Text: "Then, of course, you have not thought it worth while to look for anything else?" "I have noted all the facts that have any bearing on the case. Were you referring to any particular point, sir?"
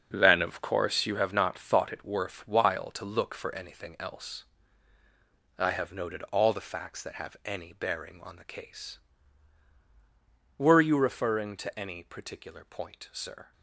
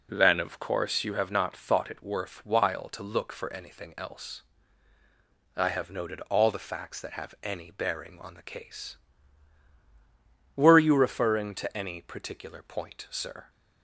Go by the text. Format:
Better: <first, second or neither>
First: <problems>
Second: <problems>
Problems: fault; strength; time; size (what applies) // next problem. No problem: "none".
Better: second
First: gets quieter; strong; throughout; 10.5 dB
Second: none